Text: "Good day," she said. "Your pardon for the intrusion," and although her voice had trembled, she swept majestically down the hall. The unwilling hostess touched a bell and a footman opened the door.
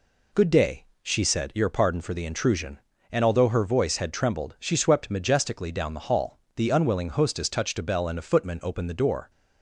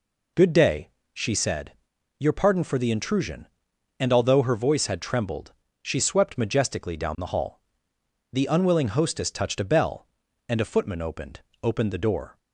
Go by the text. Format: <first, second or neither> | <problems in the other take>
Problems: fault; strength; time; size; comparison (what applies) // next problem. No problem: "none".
first | says "opened" twice; at 11.6 s